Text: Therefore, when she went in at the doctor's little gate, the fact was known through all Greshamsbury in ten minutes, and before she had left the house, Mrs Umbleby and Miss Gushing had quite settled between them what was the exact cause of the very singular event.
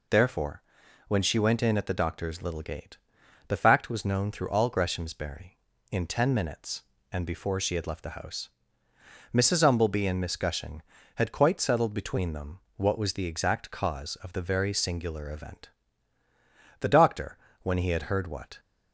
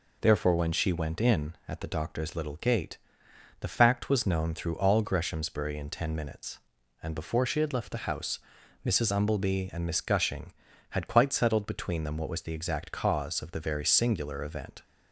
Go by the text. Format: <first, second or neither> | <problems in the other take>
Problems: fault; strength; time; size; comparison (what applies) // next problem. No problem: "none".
second | pauses between "them" and "what"; slight; at 12.5 s; 0.16 s long // goes on to say "The doctor when he had heard what"; strong; from 16.7 s on; 1.8 s long